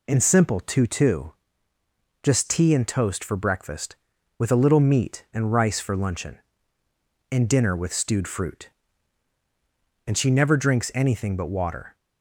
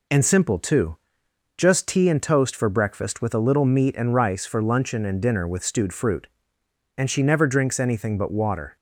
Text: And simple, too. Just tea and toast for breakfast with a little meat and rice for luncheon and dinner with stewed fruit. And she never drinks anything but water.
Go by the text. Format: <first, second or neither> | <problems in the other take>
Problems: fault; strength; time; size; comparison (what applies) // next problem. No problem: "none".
second | says "too" twice; at 0.8 s